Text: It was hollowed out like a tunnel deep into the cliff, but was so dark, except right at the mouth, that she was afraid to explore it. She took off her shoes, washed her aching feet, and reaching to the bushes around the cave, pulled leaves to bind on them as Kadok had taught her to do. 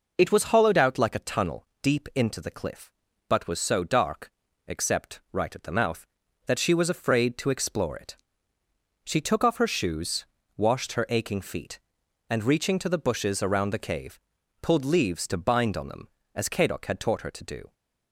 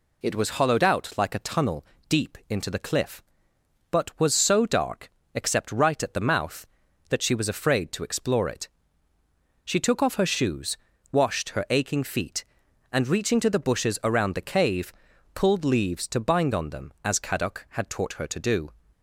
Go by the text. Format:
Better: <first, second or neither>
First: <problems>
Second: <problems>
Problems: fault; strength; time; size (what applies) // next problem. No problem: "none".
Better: neither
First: pauses between "tunnel" and "deep"; slight; at 1.6 s; 0.16 s long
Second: pauses between "tunnel" and "deep"; slight; at 1.8 s; 0.24 s long